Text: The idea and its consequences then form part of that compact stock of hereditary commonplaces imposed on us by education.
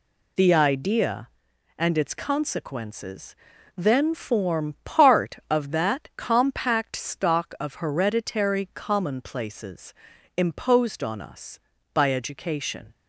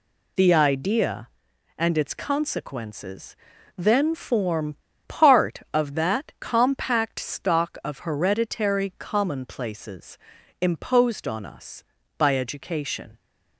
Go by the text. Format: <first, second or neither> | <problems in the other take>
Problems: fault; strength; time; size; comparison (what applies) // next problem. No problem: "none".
first | pauses between "consequences" and "then"; at 3.3 s; 0.42 s long; also in the first // pauses between "form" and "part"; slight; at 4.7 s; 0.33 s long // pauses between "commonplaces" and "imposed"; at 10.1 s; 0.42 s long; also in the first